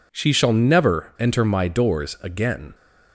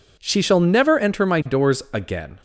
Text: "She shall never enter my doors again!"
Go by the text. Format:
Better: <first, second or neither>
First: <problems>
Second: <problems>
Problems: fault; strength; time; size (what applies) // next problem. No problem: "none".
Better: neither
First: none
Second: none